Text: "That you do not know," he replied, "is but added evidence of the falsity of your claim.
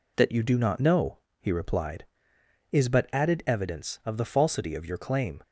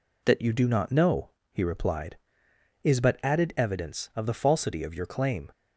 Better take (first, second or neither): neither